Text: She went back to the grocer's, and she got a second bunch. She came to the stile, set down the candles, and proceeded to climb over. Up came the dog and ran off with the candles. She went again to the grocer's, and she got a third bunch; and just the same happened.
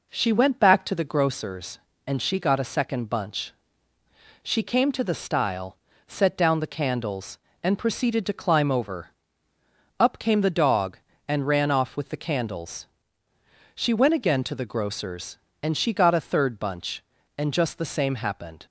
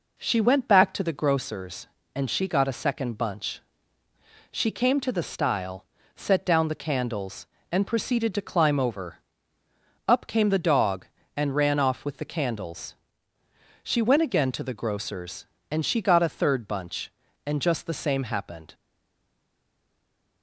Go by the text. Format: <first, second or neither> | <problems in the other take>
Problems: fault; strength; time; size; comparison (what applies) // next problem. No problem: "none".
first | stays silent after the last word; noticeable; from 18.7 s on; 1.7 s long